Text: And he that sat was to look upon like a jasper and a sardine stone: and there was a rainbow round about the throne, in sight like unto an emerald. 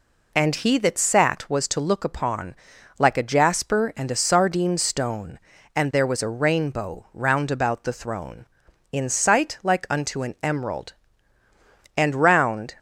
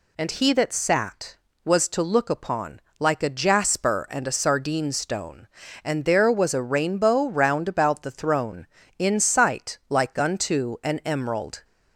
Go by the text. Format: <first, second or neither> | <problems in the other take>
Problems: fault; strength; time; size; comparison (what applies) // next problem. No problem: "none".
second | pauses between "upon" and "like"; at 2.5 s; 0.44 s long; slight in the second // goes on to say "And round"; noticeable; from 11.9 s on; 0.82 s long